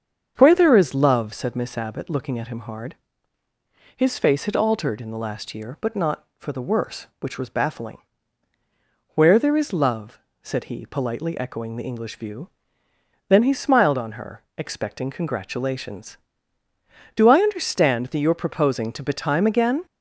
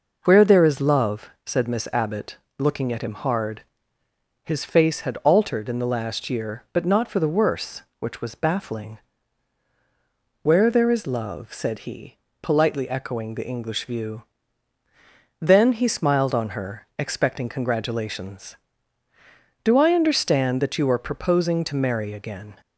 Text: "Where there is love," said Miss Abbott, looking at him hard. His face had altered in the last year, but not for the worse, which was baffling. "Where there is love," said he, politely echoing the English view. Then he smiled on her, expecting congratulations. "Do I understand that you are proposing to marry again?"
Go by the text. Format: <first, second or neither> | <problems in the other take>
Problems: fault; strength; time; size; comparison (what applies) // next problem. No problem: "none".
second | starts louder than the rest; strong; until 1.3 s; 7 dB // says "betime" for "marry"; at 19.0 s